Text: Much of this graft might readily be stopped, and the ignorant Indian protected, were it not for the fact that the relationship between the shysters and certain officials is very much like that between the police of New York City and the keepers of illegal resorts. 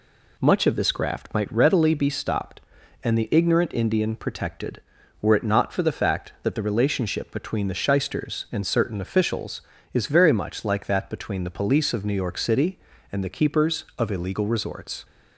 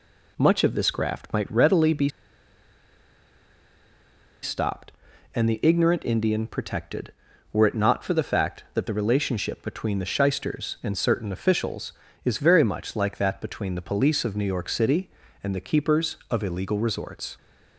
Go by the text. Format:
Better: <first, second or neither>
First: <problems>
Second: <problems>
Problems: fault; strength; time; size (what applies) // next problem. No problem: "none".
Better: first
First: none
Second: pauses between "be" and "stopped"; strong; at 2.0 s; 2.3 s long